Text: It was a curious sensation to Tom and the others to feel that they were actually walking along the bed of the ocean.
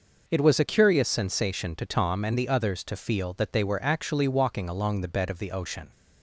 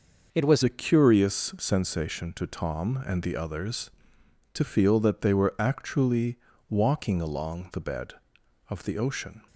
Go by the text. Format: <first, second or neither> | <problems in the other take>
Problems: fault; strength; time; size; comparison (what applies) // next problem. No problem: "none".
first | changes voice at "a"; from 0.6 s on; 8.8 s long // pauses between "actually" and "walking"; slight; at 6.3 s; 0.32 s long